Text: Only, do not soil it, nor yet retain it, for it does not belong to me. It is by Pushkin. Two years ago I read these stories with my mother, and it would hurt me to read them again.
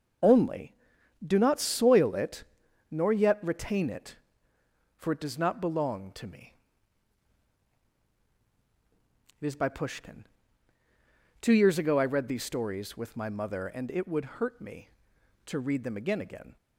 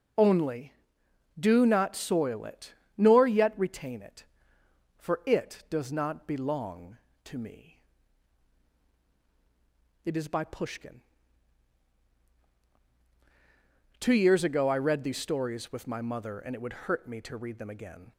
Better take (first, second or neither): second